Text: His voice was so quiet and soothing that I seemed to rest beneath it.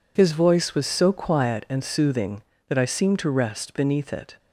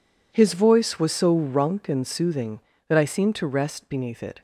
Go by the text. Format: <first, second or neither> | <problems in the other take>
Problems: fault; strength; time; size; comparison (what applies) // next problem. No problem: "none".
first | says "runk" for "quiet"; at 1.3 s